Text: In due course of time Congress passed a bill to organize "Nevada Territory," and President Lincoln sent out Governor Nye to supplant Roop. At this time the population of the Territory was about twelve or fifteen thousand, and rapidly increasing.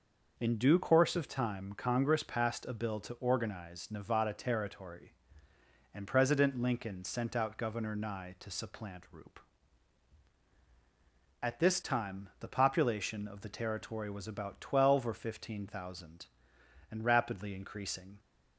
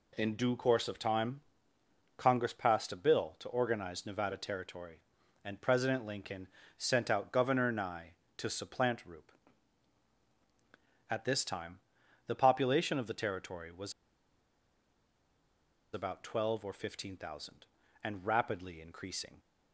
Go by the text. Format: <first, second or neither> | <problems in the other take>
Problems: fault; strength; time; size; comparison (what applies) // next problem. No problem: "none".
first | pauses between "time" and "Congress"; noticeable; at 1.3 s; 0.78 s long // pauses between "Lincoln" and "sent"; slight; at 6.4 s; 0.32 s long // pauses between "time" and "the"; noticeable; at 11.7 s; 0.48 s long // pauses between "was" and "about"; strong; at 13.9 s; 2.0 s long